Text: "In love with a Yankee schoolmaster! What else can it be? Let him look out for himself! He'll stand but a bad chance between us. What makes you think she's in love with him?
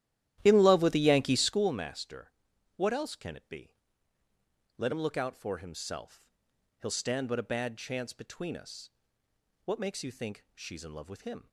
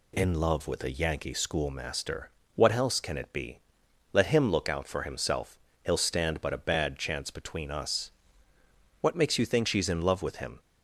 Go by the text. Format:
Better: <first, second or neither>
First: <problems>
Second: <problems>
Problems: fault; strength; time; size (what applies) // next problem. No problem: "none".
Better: second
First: starts louder than the rest; strong; until 1.8 s; 13 dB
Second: none